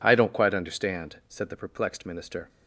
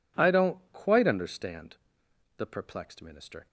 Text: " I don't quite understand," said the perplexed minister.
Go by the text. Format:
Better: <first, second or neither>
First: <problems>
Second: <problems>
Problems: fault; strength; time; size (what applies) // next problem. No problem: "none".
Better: first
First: none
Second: skips "said"; at 2.0 s